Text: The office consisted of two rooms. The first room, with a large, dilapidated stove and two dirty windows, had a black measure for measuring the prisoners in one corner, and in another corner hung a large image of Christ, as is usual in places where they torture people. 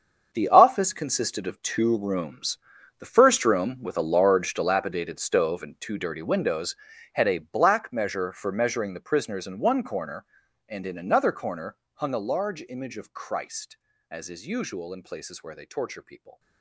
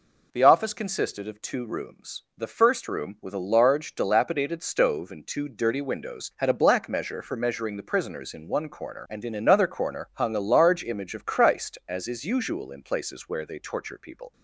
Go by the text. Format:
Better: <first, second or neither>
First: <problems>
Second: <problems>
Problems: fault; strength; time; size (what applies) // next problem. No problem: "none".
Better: second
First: gets quieter; strong; throughout; 14 dB // pauses between "corner" and "hung"; slight; at 11.7 s; 0.16 s long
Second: none